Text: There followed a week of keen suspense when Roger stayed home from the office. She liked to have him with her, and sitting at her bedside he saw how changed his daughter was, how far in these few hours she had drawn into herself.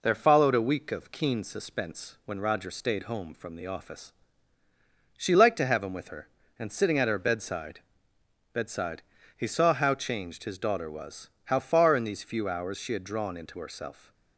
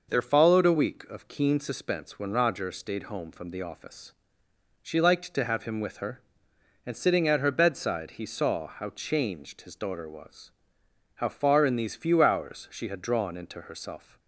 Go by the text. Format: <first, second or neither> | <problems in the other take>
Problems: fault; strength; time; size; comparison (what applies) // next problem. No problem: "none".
second | says "bedside" twice; at 8.5 s